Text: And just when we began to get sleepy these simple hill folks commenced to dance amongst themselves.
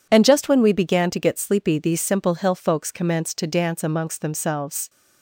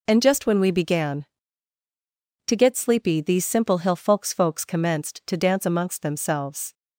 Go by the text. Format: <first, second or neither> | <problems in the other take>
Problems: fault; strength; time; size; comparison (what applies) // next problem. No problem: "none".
first | says "folks" twice; at 4.3 s